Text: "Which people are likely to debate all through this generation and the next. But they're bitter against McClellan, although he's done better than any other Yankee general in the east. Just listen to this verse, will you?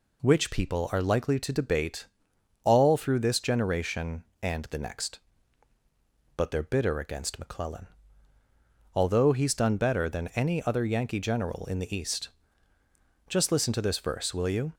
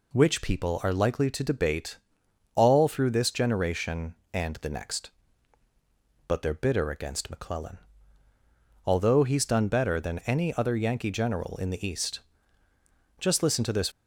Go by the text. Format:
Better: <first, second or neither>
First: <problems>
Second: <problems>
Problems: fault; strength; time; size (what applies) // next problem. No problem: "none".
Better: first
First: pauses between "debate" and "all"; noticeable; at 2.0 s; 0.58 s long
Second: pauses between "debate" and "all"; noticeable; at 1.9 s; 0.58 s long // stops before "verse will you"; at 13.9 s